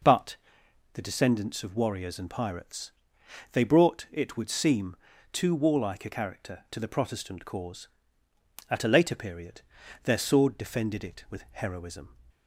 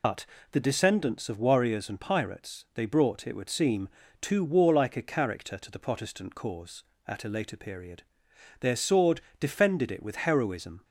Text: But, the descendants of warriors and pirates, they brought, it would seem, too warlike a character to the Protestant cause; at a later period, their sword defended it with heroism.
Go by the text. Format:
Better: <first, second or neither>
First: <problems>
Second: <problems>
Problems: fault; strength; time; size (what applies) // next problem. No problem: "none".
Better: first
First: none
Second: loses the start of "But"; at 0.0 s; 115 ms // pauses between "sword" and "defended"; slight; at 9.2 s; 0.20 s long